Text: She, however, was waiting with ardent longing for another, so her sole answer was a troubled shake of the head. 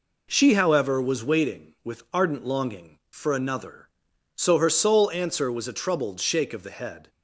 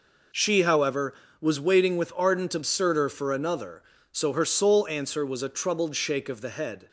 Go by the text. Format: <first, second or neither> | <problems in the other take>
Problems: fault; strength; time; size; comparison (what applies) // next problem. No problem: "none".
first | says "absurder" for "longing"; at 2.5 s